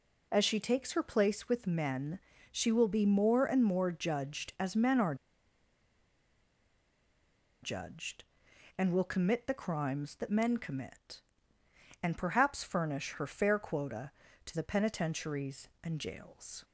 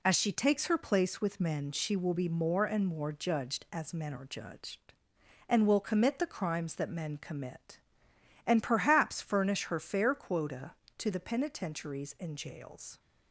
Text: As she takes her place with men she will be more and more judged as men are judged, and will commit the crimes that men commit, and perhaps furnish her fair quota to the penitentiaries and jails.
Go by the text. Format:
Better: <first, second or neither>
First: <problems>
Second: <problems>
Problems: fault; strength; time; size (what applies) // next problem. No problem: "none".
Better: second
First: pauses between "men" and "she"; slight; at 2.1 s; 0.32 s long // pauses between "are" and "judged"; strong; at 5.1 s; 2.4 s long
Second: none